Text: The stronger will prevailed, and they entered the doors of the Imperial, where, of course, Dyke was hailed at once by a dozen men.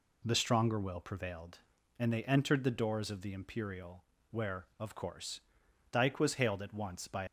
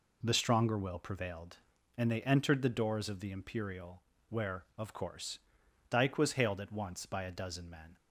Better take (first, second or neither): second